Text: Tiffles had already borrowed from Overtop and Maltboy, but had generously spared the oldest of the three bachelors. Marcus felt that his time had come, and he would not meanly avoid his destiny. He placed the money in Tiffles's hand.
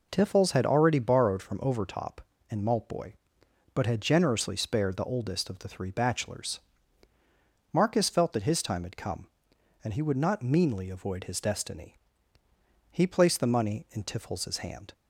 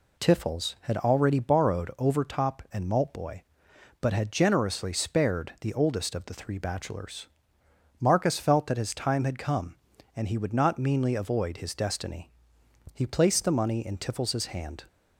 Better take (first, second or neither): first